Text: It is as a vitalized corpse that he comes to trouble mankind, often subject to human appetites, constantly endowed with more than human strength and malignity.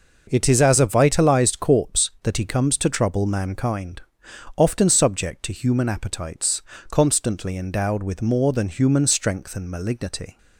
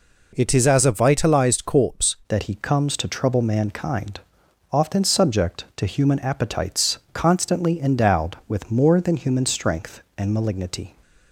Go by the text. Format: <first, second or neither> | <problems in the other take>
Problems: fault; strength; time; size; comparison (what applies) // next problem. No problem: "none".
first | changes voice at "that"; from 2.2 s on; 8.7 s long